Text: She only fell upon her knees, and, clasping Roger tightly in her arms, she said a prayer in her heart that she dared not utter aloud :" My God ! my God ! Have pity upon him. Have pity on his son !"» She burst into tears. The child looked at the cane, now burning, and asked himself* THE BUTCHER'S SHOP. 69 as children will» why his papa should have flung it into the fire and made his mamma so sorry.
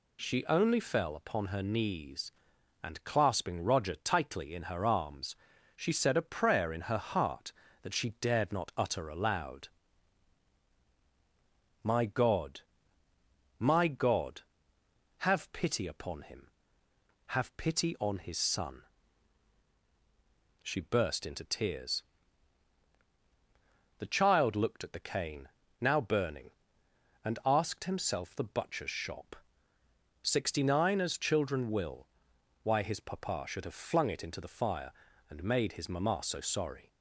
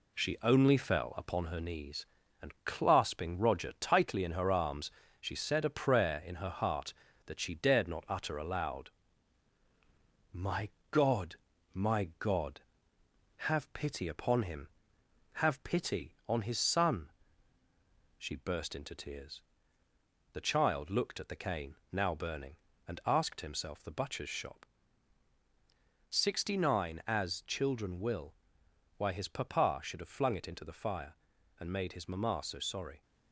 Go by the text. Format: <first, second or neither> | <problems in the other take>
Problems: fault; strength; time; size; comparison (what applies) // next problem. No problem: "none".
first | gets quieter; throughout; 3.5 dB // pauses between "My" and "God"; slight; at 10.6 s; 0.22 s long // pauses between "will" and "why"; noticeable; at 28.3 s; 0.60 s long; noticeable in the first